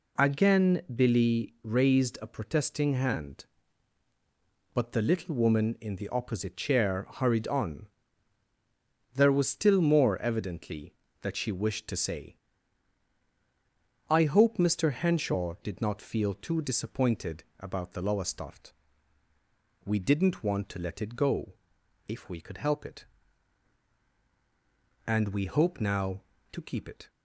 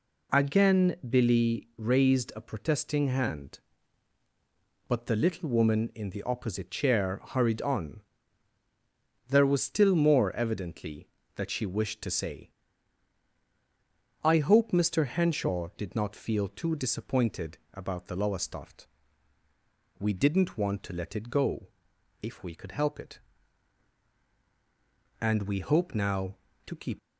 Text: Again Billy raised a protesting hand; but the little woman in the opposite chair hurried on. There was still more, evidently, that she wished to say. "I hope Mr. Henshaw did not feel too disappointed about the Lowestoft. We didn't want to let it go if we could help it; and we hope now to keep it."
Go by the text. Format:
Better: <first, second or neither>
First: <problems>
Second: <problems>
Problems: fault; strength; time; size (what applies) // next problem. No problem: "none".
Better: first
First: pauses between "disappointed" and "about"; slight; at 17.4 s; 0.16 s long // pauses between "go" and "if"; noticeable; at 21.5 s; 0.52 s long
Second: pauses between "disappointed" and "about"; slight; at 17.5 s; 0.16 s long // pauses between "go" and "if"; noticeable; at 21.6 s; 0.52 s long // stops before "it"; at 26.9 s